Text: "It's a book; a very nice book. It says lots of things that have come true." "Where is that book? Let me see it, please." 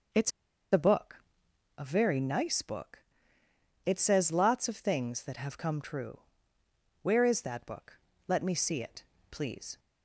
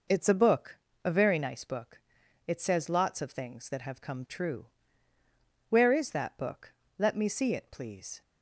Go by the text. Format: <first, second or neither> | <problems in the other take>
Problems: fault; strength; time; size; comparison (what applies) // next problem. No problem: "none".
second | pauses between "It's" and "a"; at 0.3 s; 0.42 s long